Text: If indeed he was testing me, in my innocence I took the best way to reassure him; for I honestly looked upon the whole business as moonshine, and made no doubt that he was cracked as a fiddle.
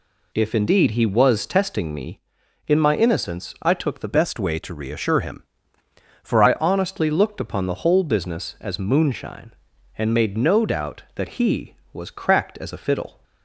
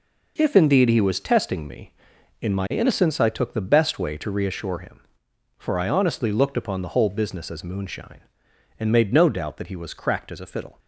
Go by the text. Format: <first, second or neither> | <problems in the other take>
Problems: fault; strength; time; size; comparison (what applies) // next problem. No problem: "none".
second | changes voice from "best" to "for"; from 4.1 to 6.4 s; 2.3 s long